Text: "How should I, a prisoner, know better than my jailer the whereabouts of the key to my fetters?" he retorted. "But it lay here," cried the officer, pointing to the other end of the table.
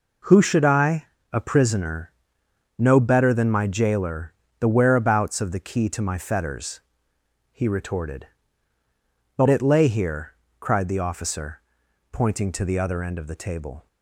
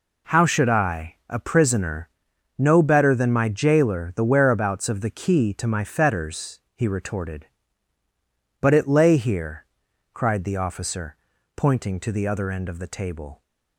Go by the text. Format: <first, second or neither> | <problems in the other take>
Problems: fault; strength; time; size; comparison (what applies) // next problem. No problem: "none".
second | says "Who" for "How"; at 0.2 s // pauses between "jailer" and "the"; slight; at 4.3 s; 0.26 s long